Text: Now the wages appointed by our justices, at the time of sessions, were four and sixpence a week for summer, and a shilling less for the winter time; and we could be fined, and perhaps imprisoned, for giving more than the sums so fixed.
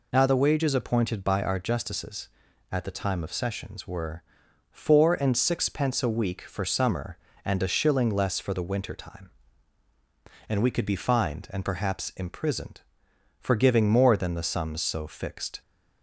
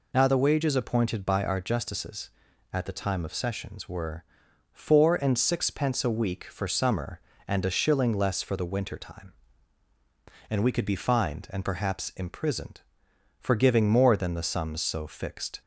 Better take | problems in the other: neither | pauses between "were" and "four"; noticeable; the same in both

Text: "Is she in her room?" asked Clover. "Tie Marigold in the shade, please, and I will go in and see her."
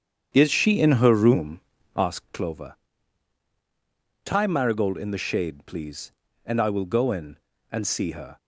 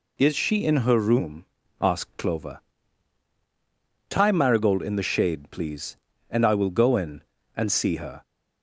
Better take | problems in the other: second | starts louder than the rest; strong; until 2.0 s; 8.5 dB

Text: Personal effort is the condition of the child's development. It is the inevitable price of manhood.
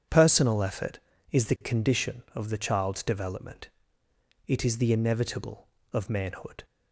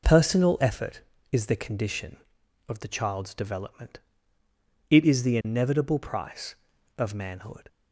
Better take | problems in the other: second | skips "price"; at 5.7 s

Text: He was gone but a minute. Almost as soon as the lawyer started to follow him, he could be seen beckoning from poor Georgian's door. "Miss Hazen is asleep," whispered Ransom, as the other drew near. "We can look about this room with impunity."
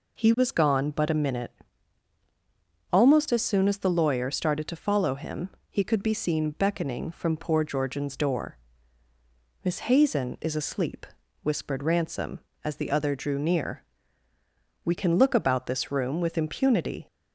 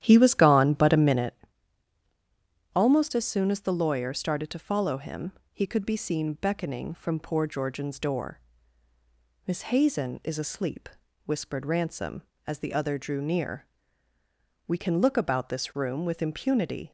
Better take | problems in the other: first | starts louder than the rest; strong; until 1.5 s; 11.5 dB

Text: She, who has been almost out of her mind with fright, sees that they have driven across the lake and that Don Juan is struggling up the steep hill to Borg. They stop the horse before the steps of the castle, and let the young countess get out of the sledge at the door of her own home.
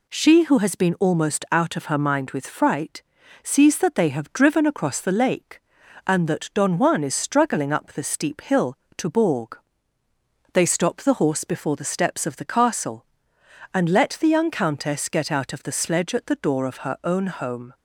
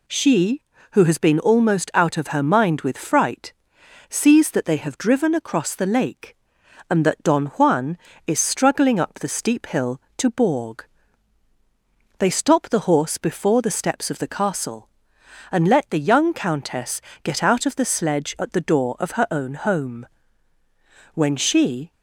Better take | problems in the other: first | pauses between "countess" and "get"; slight; at 17.0 s; 0.22 s long // goes on to say "When she"; noticeable; from 21.1 s on; 0.78 s long

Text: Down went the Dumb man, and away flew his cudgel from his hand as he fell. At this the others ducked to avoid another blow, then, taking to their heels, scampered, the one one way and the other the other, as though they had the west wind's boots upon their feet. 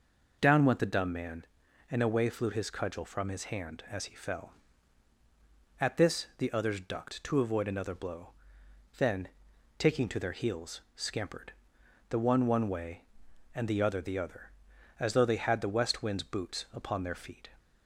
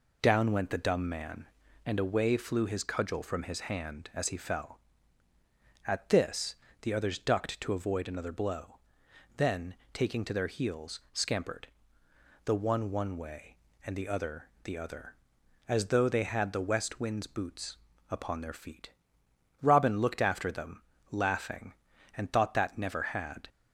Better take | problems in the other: first | pauses between "this" and "the"; slight; at 6.5 s; 0.26 s long // pauses between "other" and "the"; slight; at 14.4 s; 0.16 s long // pauses between "boots" and "upon"; slight; at 17.7 s; 0.32 s long // goes on to say "Robin looked after them laughing and thought that never had"; strong; from 19.6 s on; 3.8 s long

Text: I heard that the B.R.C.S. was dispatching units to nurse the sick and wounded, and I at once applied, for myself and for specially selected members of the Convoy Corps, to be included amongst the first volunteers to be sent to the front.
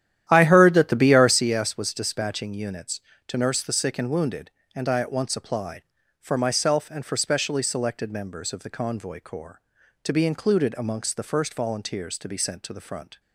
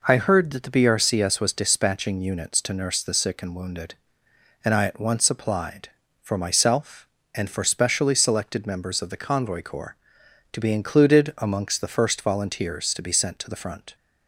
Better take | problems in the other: second | starts louder than the rest; strong; until 1.5 s; 11.5 dB

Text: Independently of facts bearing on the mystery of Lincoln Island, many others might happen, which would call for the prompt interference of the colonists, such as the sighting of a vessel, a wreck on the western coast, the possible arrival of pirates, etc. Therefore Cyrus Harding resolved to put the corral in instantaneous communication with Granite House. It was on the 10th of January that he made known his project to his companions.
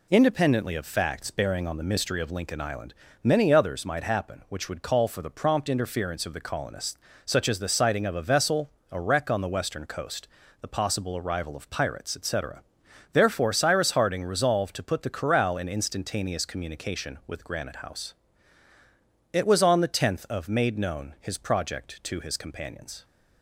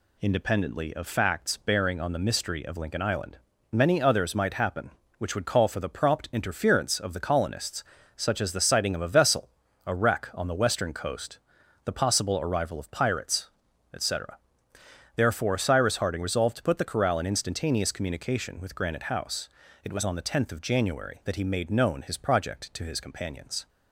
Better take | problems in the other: second | skips "January that he"; at 20.4 s

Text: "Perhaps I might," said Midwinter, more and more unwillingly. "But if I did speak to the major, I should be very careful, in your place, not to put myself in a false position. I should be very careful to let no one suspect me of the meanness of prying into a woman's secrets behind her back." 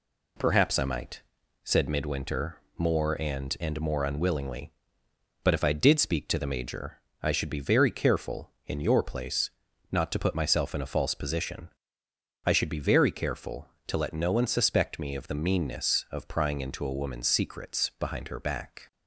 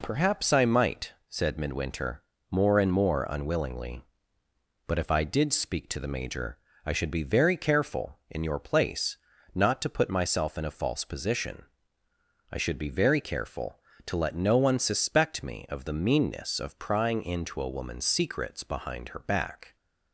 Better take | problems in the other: second | says "and" twice; at 3.5 s

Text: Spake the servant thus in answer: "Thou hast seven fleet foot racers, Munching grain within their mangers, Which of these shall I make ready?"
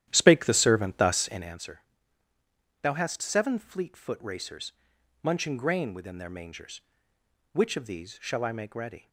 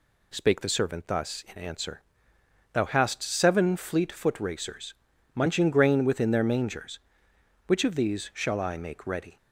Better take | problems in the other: second | starts louder than the rest; strong; until 1.6 s; 11.5 dB

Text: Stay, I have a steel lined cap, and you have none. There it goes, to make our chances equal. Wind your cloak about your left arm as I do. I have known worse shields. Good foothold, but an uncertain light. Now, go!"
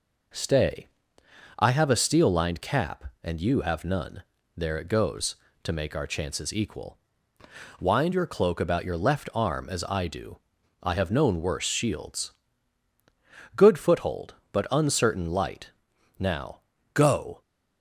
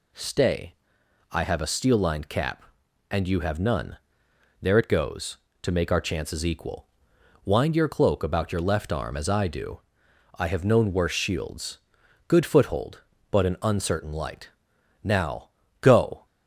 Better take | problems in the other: second | skips "an"; at 14.6 s

